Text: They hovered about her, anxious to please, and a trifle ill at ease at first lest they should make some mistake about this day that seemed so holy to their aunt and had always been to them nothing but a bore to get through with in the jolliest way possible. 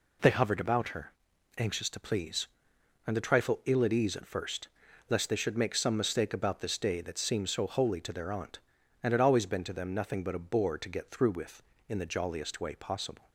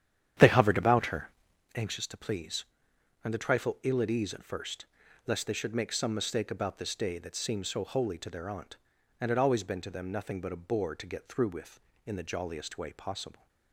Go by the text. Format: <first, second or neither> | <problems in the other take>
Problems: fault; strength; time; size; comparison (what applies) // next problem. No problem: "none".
first | starts louder than the rest; strong; until 1.7 s; 10 dB // pauses between "first" and "lest"; at 4.8 s; 0.40 s long; also in the first